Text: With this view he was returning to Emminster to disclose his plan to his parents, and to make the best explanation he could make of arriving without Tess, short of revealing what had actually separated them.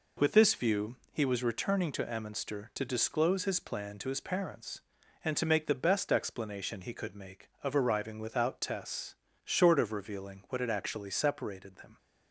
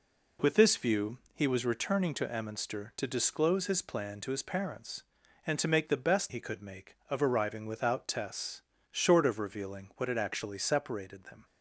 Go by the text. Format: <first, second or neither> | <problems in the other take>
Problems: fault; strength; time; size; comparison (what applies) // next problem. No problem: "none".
first | pauses between "view" and "he"; slight; at 1.1 s; 0.16 s long; slight in the first // skips "explanation"; at 6.3 s